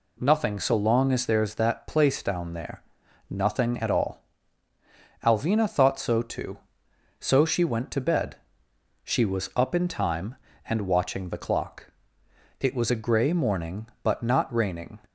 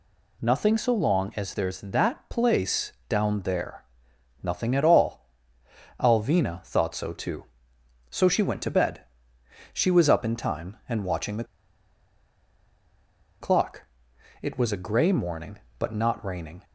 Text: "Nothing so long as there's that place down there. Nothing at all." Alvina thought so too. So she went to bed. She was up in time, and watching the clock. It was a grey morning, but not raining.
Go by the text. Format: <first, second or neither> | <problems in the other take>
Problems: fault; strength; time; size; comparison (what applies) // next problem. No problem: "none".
first | pauses between "place" and "down"; slight; at 2.9 s; 0.16 s long // pauses between "the" and "clock"; strong; at 11.4 s; 1.9 s long